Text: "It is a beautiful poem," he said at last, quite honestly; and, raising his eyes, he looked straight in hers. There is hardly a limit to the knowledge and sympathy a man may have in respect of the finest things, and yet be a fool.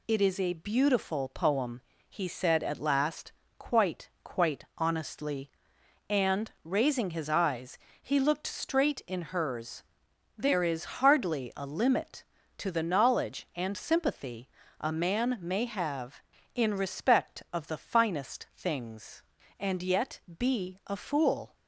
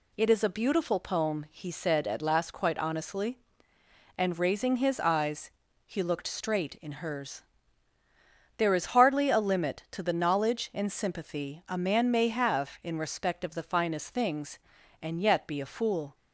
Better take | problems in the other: second | says "quite" twice; at 4.2 s // pauses between "sympathy" and "a"; slight; at 14.5 s; 0.28 s long // pauses between "yet" and "be"; slight; at 20.2 s; 0.16 s long

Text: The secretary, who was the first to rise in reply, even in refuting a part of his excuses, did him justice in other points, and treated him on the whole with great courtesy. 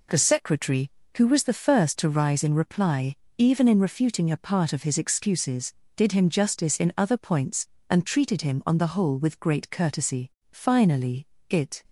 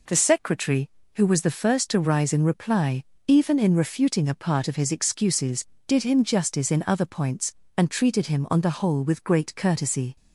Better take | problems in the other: second | goes on to say "Finally it"; from 10.4 s on; 1.3 s long

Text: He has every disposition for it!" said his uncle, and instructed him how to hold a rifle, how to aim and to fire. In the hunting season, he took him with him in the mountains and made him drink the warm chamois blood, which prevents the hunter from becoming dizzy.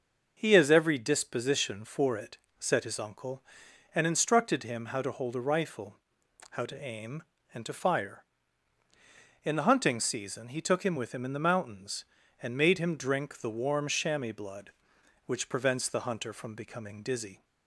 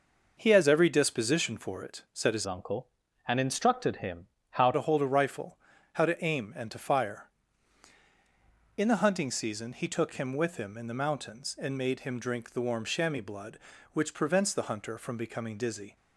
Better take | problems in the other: first | changes voice from "uncle" to "how"; from 2.4 to 4.7 s; 2.3 s long // pauses between "him" and "how"; slight; at 4.2 s; 0.24 s long

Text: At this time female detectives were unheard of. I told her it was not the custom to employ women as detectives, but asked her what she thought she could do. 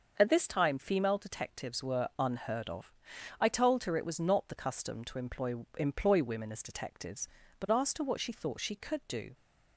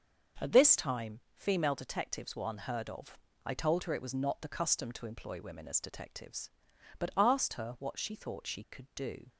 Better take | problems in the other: second | starts louder than the rest; until 1.1 s; 6.5 dB; also in the second // says "employ" twice; at 5.7 s

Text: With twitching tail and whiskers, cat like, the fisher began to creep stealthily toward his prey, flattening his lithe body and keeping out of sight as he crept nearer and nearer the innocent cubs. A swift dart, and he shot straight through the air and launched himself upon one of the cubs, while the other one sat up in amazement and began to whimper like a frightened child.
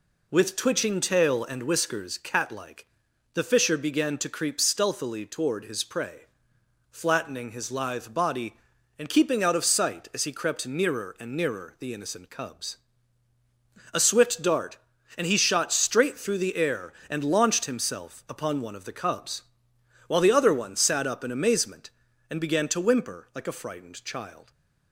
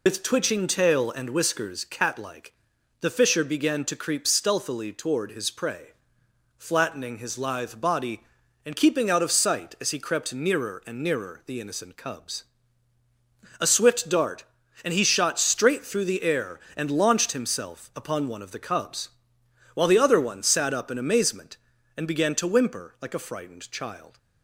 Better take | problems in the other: first | loses the start of "With"; at 0.0 s; 80 ms

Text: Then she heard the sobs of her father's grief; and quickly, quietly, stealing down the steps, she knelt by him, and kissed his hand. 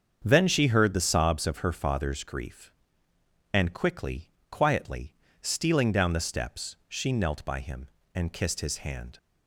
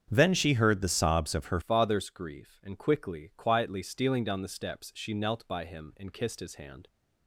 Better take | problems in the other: first | starts louder than the rest; strong; until 1.1 s; 8 dB; strong in the first // changes voice at "father's"; from 1.6 s on; 5.2 s long

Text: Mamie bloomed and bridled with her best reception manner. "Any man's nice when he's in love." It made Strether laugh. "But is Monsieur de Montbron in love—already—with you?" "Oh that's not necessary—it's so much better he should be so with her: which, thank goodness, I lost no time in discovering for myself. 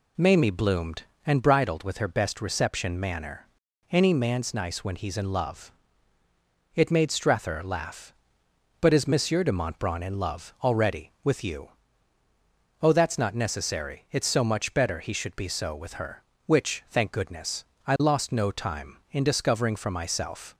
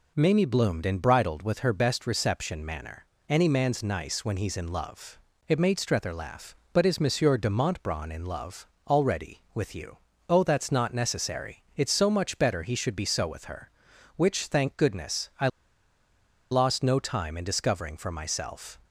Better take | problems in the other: first | pauses between "I" and "lost"; at 15.4 s; 1.0 s long

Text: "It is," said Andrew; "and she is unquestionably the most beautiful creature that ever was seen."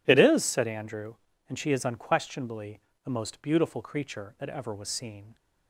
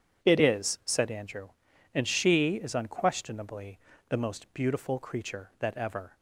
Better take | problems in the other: first | starts louder than the rest; strong; until 1.3 s; 8.5 dB // pauses between "unquestionably" and "the"; slight; at 3.7 s; 0.30 s long; slight in the first // stops before "was seen"; at 6.1 s

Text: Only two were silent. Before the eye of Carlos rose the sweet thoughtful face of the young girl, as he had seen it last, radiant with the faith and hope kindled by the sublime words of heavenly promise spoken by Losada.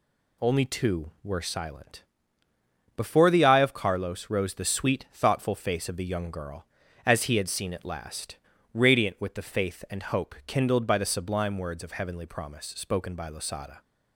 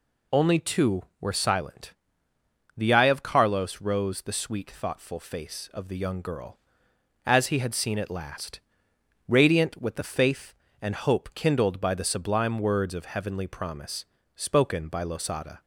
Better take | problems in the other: first | skips "Before"; at 2.3 s // pauses between "promise" and "spoken"; slight; at 14.0 s; 0.30 s long

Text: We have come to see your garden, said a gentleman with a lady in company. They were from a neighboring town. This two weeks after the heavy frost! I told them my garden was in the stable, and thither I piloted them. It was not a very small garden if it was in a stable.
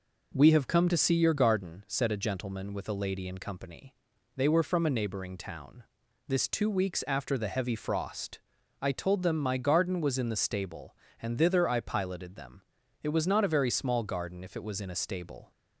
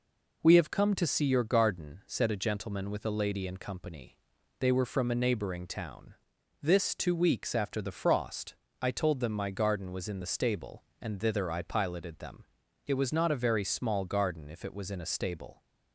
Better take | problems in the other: first | skips "heavy"; at 7.9 s

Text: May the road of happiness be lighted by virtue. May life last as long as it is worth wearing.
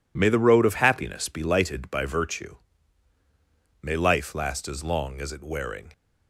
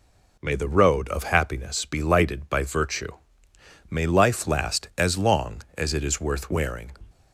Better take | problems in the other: second | skips "is worth"; at 5.4 s

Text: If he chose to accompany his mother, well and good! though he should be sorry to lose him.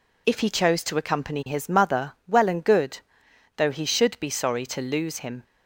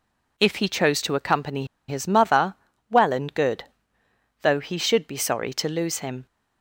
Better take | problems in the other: first | pauses between "accompany" and "his"; slight; at 1.6 s; 0.23 s long

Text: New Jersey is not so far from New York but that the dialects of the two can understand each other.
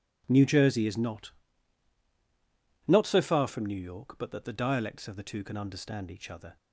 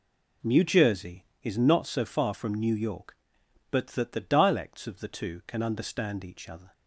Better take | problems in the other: second | says "not" twice; at 2.8 s

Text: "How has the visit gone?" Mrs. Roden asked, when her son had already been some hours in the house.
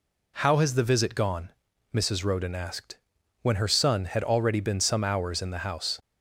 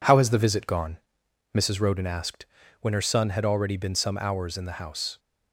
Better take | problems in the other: first | gets quieter; noticeable; throughout; 5 dB

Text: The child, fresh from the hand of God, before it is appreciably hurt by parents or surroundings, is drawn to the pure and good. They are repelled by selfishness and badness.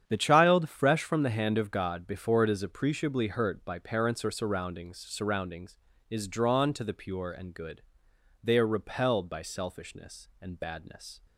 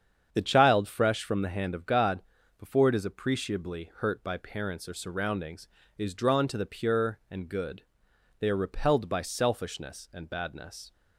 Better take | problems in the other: second | starts louder than the rest; strong; until 1.0 s; 9 dB; strong in the second // says "surroundings" twice; at 4.9 s

